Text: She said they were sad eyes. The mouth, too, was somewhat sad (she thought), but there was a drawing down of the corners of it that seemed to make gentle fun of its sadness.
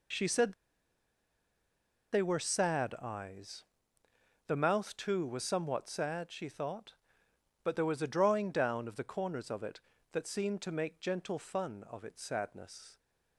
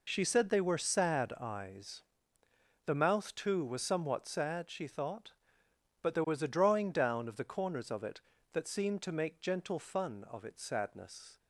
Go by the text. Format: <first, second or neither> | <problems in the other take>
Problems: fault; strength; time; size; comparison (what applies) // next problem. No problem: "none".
second | pauses between "said" and "they"; strong; at 0.5 s; 1.6 s long